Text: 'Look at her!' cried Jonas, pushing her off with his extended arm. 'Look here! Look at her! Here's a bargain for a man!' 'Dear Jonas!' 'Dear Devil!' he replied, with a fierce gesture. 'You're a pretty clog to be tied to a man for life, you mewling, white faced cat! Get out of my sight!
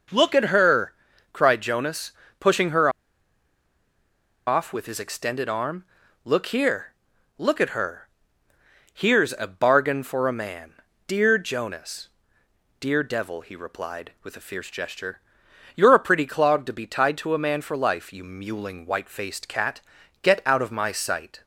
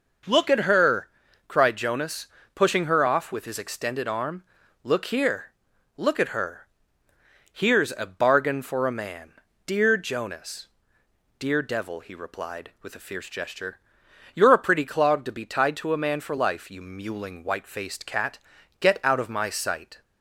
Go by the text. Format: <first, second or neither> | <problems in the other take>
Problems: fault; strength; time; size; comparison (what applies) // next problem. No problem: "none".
second | pauses between "her" and "off"; strong; at 2.8 s; 1.5 s long